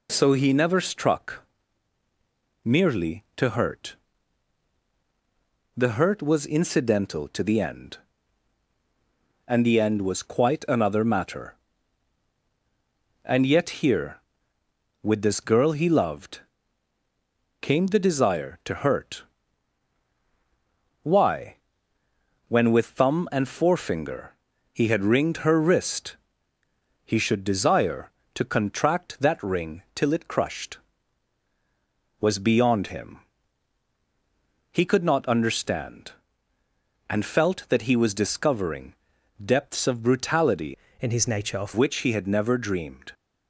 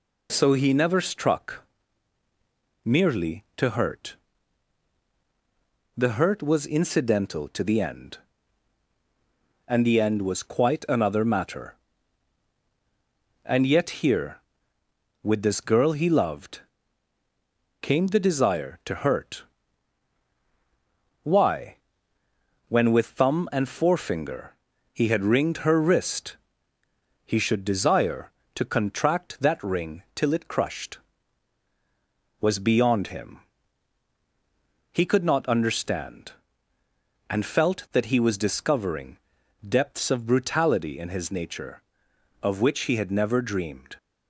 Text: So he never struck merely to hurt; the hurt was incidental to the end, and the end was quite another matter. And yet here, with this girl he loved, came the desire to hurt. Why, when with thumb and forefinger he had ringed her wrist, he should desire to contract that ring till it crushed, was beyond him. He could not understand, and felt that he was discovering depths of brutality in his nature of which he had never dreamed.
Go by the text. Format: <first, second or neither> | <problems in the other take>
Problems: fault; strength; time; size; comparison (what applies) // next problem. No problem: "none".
second | pauses between "struck" and "merely"; at 1.4 s; 1.1 s long; also in the second // pauses between "forefinger" and "he"; at 24.3 s; 0.38 s long; also in the second // pauses between "discovering" and "depths"; noticeable; at 38.9 s; 0.50 s long; noticeable in the second // changes voice from "in" to "of"; from 40.9 to 41.7 s; 0.8 s long